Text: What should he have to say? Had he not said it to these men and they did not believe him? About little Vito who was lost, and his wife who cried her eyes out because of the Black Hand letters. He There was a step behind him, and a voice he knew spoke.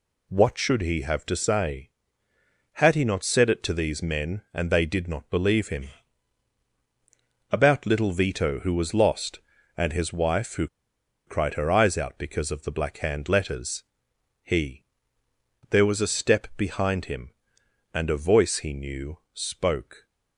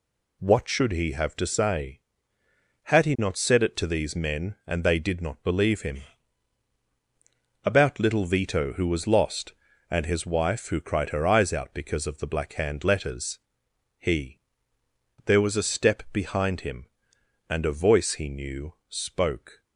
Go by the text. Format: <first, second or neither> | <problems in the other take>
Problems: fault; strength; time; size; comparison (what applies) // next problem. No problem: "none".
second | pauses between "who" and "cried"; noticeable; at 10.6 s; 0.58 s long // pauses between "He" and "There"; noticeable; at 14.8 s; 0.86 s long; noticeable in the second // pauses between "knew" and "spoke"; slight; at 19.1 s; 0.16 s long; slight in the second